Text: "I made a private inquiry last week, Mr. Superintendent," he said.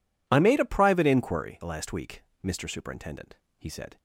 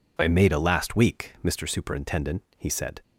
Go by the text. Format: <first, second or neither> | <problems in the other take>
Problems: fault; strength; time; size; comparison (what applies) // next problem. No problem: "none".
first | skips "private inquiry"; at 0.5 s